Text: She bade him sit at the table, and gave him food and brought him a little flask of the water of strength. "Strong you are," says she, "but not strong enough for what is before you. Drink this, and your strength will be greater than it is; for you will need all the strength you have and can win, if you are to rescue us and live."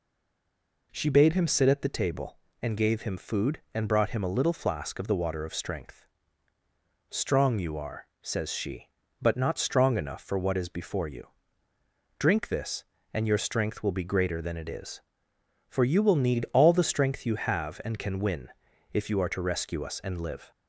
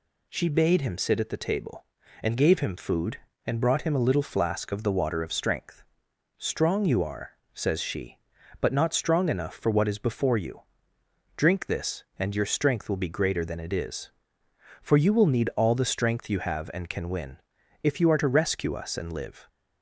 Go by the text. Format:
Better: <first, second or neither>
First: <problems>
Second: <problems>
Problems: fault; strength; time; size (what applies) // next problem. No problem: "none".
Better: second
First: stays silent before the first word; slight; until 0.9 s; 0.9 s long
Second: none